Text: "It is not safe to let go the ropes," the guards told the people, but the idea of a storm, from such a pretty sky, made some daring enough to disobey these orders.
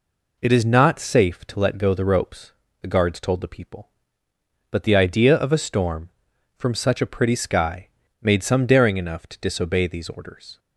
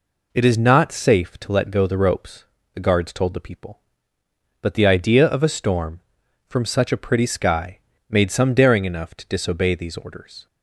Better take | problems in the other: neither | none

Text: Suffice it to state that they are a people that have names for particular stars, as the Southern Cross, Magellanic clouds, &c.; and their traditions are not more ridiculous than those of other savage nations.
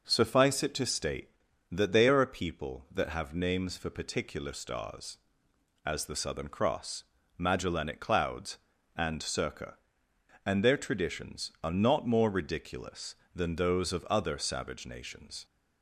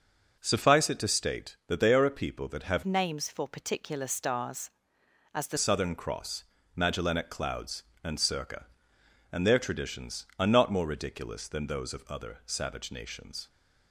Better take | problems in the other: first | starts louder than the rest; until 1.4 s; 6.5 dB // changes voice from "names" to "the"; from 2.8 to 5.5 s; 2.7 s long

